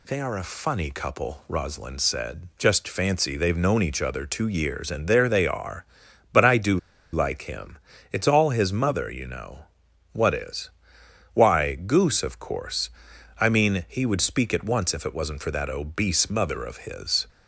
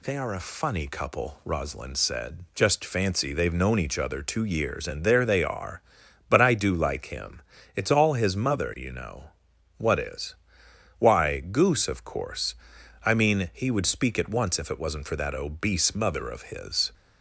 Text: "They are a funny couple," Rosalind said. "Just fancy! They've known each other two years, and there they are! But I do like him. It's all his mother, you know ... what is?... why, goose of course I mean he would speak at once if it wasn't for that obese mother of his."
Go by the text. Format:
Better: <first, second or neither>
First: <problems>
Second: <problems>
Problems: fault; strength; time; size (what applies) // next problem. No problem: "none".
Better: second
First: pauses between "do" and "like"; slight; at 6.7 s; 0.35 s long // pauses between "course" and "I"; noticeable; at 12.8 s; 0.52 s long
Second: pauses between "course" and "I"; noticeable; at 12.5 s; 0.52 s long